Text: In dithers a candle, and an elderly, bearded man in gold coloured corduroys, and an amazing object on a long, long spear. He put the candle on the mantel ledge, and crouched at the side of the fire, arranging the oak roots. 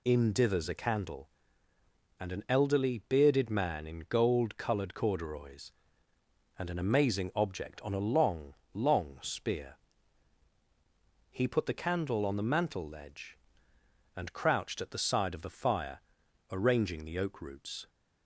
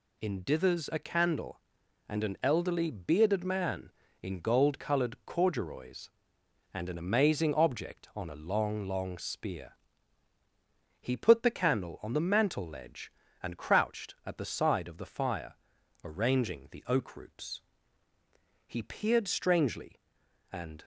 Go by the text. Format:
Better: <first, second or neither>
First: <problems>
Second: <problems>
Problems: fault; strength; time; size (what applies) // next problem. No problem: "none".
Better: first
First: none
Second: goes on to say "He peered strangely and"; strong; from 18.6 s on; 2.1 s long